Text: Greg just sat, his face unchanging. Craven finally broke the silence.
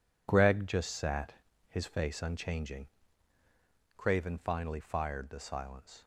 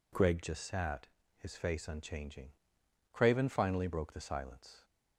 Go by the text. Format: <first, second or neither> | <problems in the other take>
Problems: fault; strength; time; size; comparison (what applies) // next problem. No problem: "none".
second | says "fired" for "broke"; at 4.8 s